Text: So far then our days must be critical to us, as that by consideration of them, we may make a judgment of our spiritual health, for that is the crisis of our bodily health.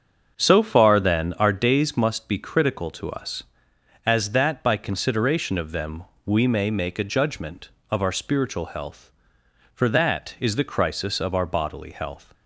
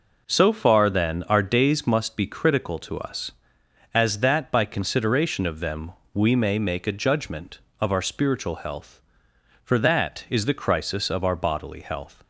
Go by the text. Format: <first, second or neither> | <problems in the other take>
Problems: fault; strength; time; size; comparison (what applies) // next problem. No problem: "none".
second | starts louder than the rest; until 1.5 s; 6.5 dB